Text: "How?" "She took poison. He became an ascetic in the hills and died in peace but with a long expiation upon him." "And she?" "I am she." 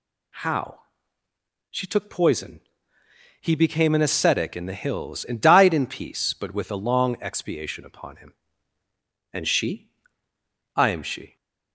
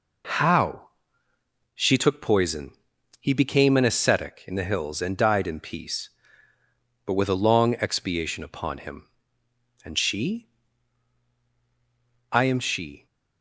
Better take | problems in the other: neither | none

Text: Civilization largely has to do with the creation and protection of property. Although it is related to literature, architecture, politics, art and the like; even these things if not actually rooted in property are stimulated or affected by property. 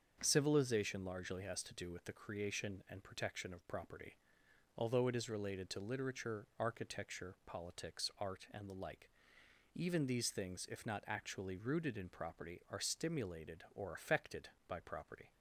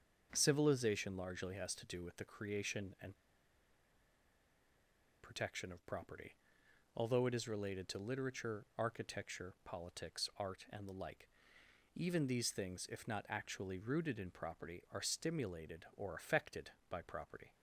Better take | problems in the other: first | starts louder than the rest; until 1.3 s; 7 dB; also in the first // pauses between "and" and "protection"; strong; at 3.1 s; 2.0 s long

